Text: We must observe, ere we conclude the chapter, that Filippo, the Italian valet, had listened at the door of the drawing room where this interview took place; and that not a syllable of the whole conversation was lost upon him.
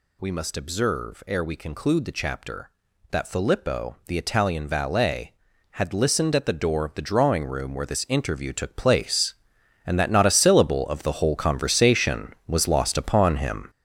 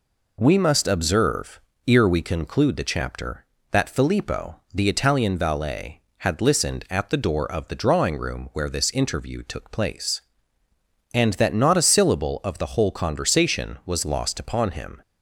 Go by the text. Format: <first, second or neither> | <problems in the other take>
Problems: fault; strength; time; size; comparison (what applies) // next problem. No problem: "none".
second | gets louder; strong; throughout; 7.5 dB